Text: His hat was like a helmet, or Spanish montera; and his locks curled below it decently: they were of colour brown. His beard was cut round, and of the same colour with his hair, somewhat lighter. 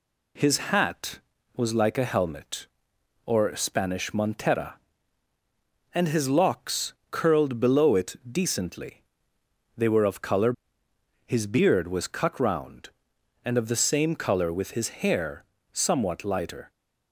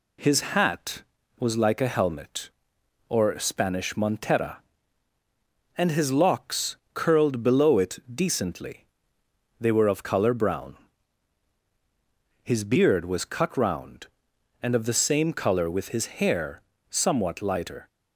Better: second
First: pauses between "locks" and "curled"; slight; at 6.9 s; 0.18 s long // skips "brown"; at 10.8 s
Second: pauses between "locks" and "curled"; slight; at 6.7 s; 0.18 s long

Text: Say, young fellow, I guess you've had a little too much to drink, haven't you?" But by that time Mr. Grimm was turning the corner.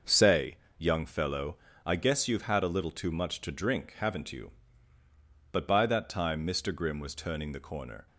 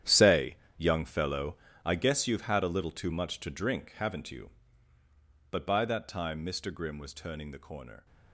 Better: first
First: starts louder than the rest; noticeable; until 1.2 s; 6 dB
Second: gets quieter; strong; throughout; 13.5 dB // starts louder than the rest; strong; until 1.2 s; 10.5 dB

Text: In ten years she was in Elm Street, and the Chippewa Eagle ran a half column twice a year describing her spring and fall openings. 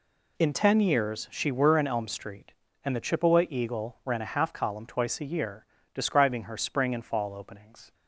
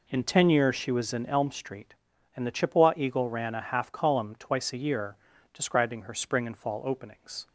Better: second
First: says "were" for "was"; at 1.4 s // pauses between "year" and "describing"; slight; at 5.6 s; 0.28 s long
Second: pauses between "year" and "describing"; slight; at 5.1 s; 0.36 s long

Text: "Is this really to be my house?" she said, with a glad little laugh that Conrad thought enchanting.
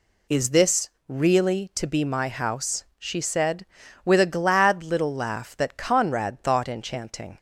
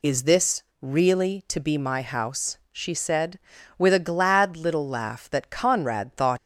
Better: first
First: pauses between "this" and "really"; slight; at 0.8 s; 0.18 s long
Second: pauses between "this" and "really"; slight; at 0.6 s; 0.18 s long // stops before "enchanting"; at 6.3 s

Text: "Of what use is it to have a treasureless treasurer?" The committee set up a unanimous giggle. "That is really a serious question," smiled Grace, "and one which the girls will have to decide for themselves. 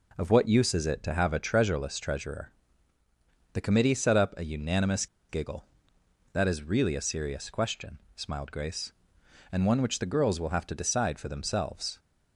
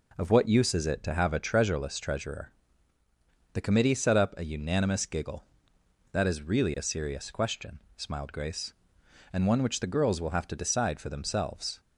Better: second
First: pauses between "unanimous" and "giggle"; slight; at 5.0 s; 0.23 s long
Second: none

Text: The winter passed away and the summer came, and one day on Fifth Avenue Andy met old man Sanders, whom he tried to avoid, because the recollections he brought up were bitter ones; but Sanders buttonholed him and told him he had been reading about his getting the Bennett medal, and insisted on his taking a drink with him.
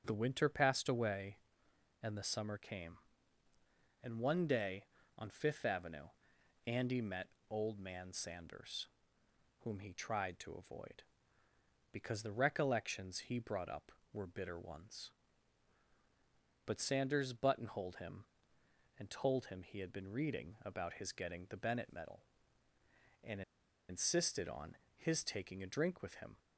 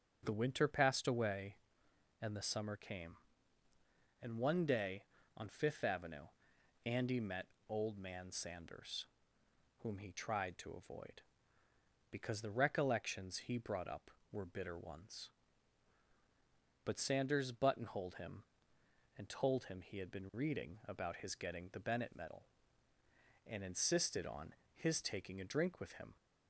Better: second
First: starts louder than the rest; until 1.0 s; 6.5 dB // pauses between "Avenue" and "Andy"; noticeable; at 6.0 s; 0.58 s long // pauses between "met" and "old"; slight; at 7.2 s; 0.20 s long // pauses between "and" and "insisted"; noticeable; at 23.4 s; 0.47 s long // pauses between "on" and "his"; slight; at 24.7 s; 0.22 s long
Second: starts louder than the rest; until 1.2 s; 6.5 dB // pauses between "Avenue" and "Andy"; noticeable; at 6.2 s; 0.58 s long // pauses between "met" and "old"; slight; at 7.4 s; 0.20 s long // pauses between "on" and "his"; slight; at 24.5 s; 0.22 s long

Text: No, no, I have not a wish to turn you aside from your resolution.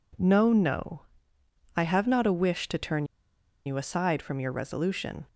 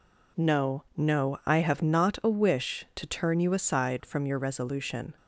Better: second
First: pauses between "turn" and "you"; noticeable; at 3.0 s; 0.62 s long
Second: none

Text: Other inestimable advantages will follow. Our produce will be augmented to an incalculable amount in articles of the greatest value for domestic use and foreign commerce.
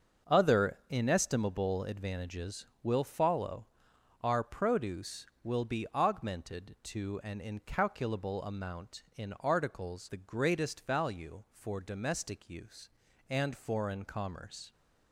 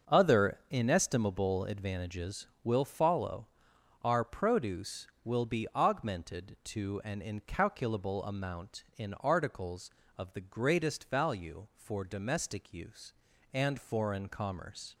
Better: second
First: starts louder than the rest; until 1.3 s; 6.5 dB // skips "of"; at 10.0 s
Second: starts louder than the rest; until 1.2 s; 6.5 dB

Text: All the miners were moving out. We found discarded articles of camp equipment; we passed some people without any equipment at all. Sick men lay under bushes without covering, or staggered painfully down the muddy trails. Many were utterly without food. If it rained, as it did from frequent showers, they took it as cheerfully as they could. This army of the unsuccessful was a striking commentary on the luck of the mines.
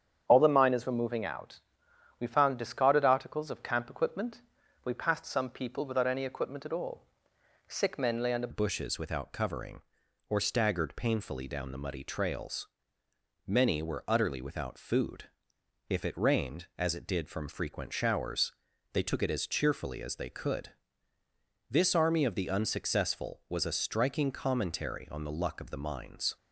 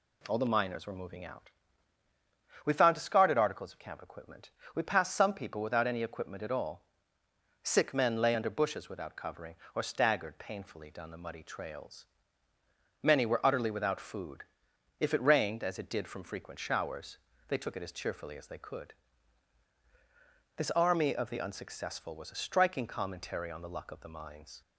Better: second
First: starts louder than the rest; strong; until 1.3 s; 8.5 dB // changes voice at "bushes"; from 8.5 s on; 17.8 s long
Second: none

